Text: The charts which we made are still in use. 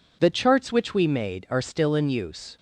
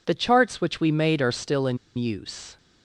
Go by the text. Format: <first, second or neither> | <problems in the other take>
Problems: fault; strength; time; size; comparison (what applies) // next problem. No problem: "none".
first | pauses between "in" and "use"; slight; at 1.7 s; 0.19 s long